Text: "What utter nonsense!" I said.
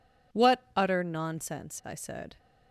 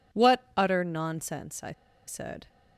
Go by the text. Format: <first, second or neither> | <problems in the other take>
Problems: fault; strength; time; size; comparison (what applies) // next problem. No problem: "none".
first | pauses between "I" and "said"; slight; at 1.7 s; 0.35 s long